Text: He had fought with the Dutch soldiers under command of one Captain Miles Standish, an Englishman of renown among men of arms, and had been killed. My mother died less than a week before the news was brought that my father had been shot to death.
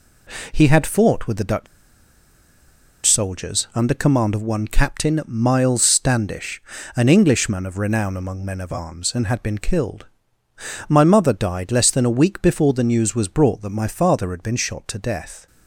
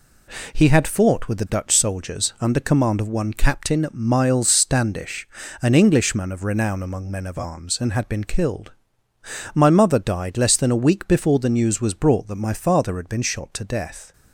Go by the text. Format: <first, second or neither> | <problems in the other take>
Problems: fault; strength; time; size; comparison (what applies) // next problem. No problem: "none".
second | pauses between "Dutch" and "soldiers"; strong; at 1.6 s; 1.3 s long